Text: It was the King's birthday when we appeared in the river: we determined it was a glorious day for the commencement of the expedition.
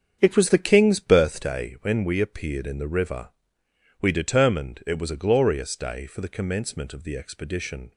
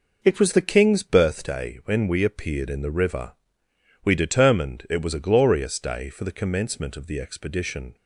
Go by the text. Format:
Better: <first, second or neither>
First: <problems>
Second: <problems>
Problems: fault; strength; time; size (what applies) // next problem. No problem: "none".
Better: second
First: starts louder than the rest; strong; until 2.1 s; 7.5 dB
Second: none